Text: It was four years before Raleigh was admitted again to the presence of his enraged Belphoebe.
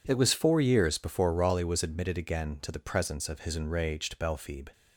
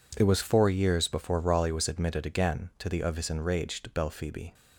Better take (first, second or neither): first